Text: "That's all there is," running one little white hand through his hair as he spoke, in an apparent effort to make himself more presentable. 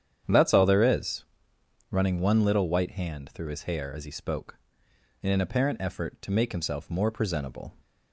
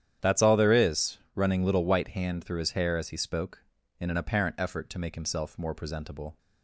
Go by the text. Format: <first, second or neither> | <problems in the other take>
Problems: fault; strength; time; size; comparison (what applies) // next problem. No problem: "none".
first | starts louder than the rest; strong; until 1.3 s; 10 dB; strong in the first // skips "one"; at 1.6 s